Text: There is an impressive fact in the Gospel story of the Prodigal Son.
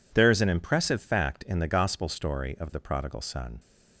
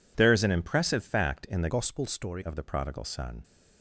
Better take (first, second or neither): first